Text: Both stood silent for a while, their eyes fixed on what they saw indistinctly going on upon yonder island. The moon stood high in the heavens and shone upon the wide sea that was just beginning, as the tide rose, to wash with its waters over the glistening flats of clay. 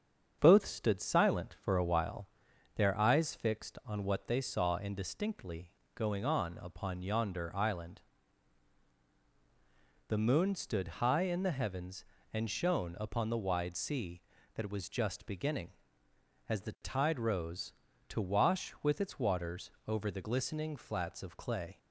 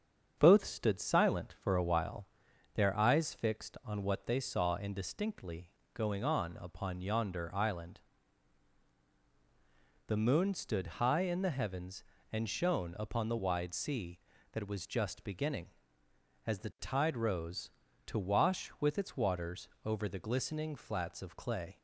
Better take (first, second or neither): neither